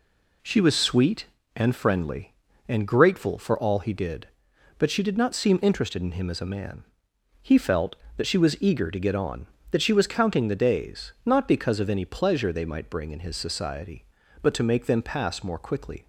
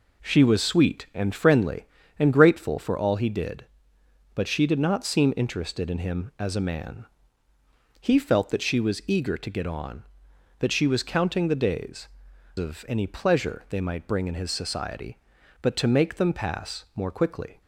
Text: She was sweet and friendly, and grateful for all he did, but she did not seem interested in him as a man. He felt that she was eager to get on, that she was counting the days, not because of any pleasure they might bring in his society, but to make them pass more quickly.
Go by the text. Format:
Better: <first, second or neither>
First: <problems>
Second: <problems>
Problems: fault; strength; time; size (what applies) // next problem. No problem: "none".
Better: first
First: none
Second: skips "not because"; at 12.3 s